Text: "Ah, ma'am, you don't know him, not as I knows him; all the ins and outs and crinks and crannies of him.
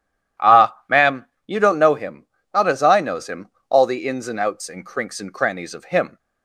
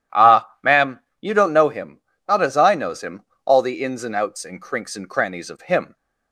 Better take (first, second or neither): neither